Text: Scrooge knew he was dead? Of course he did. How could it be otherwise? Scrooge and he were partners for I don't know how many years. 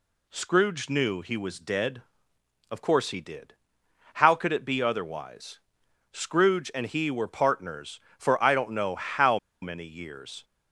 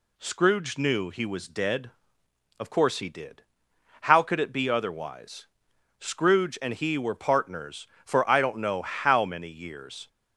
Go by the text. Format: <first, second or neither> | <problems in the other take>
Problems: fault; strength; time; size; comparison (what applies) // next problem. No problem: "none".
second | pauses between "how" and "many"; slight; at 9.3 s; 0.24 s long